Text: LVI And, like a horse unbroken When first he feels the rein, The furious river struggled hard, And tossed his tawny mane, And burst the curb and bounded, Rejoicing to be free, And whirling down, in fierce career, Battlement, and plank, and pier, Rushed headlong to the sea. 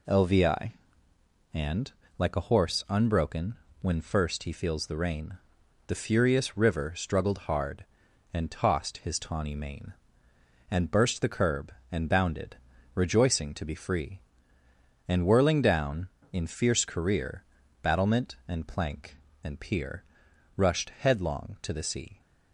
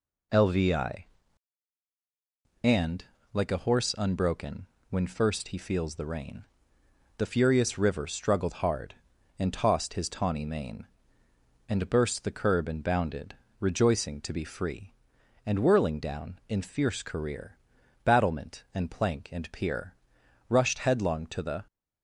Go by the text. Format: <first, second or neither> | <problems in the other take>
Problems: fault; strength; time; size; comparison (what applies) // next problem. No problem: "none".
first | pauses between "unbroken" and "When"; slight; at 4.6 s; 0.24 s long; slight in the first // stops before "sea"; at 21.6 s